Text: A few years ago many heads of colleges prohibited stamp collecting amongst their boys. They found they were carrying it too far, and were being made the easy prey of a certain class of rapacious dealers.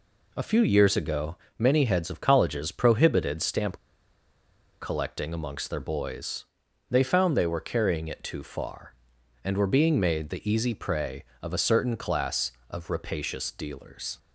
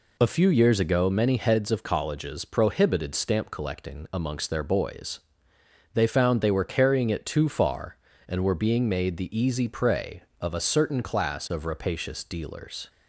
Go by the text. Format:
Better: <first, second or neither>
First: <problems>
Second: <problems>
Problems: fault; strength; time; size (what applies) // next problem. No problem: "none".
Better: second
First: pauses between "ago" and "many"; slight; at 1.3 s; 0.22 s long // pauses between "stamp" and "collecting"; at 3.7 s; 1.0 s long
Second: none